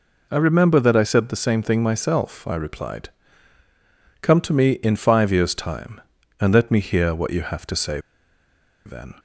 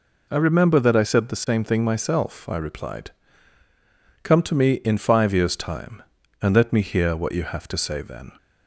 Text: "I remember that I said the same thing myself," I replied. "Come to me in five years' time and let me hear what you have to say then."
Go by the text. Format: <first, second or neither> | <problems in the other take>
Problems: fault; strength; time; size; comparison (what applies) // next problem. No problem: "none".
second | pauses between "say" and "then"; noticeable; at 7.9 s; 0.85 s long